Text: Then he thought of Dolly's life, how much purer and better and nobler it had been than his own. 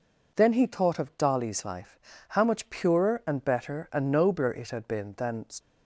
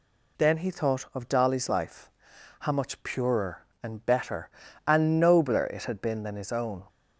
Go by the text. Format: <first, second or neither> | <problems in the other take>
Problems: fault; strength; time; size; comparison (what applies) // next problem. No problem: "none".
second | stops before "his own"; at 5.5 s